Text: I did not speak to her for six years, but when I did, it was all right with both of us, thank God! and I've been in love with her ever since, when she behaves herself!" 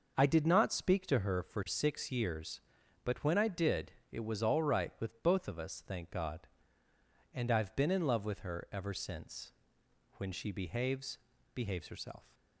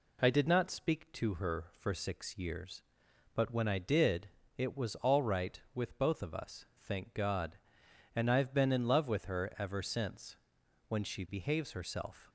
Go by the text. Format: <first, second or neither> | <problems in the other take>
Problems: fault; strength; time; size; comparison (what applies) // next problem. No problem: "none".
second | says "behaves" twice; at 11.5 s